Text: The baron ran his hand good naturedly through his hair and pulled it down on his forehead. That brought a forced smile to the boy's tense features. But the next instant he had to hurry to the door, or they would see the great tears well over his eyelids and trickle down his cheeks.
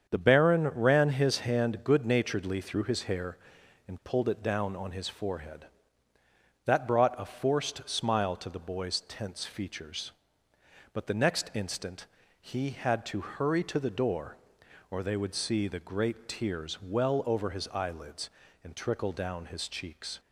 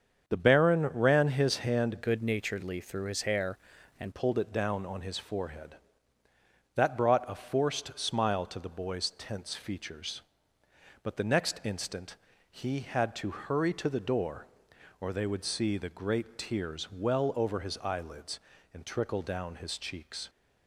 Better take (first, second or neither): first